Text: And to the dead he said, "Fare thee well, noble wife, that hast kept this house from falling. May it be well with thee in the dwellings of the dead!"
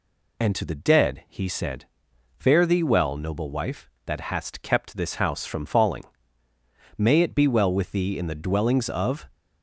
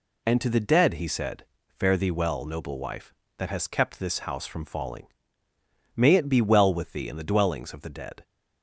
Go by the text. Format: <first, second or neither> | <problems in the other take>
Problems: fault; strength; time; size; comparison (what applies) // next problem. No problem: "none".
second | stops before "the dead"; at 9.3 s